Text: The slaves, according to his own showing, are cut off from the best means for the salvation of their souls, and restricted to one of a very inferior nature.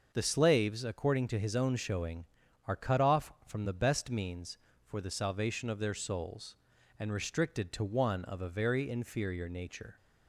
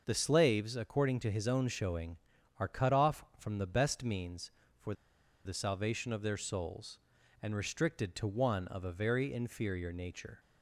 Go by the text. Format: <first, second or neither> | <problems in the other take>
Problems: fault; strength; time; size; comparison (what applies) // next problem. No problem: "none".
first | starts louder than the rest; noticeable; until 1.0 s; 6 dB; noticeable in the first // pauses between "for" and "the"; noticeable; at 4.9 s; 0.50 s long